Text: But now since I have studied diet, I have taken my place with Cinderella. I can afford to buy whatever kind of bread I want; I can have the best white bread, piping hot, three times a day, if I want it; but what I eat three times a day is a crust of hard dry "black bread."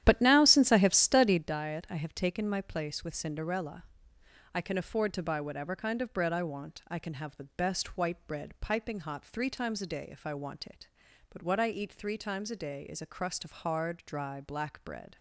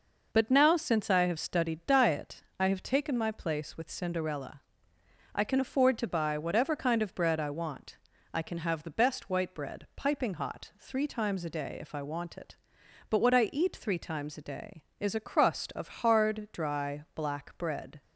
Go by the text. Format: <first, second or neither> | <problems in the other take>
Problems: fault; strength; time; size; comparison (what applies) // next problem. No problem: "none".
second | starts louder than the rest; strong; until 1.5 s; 11 dB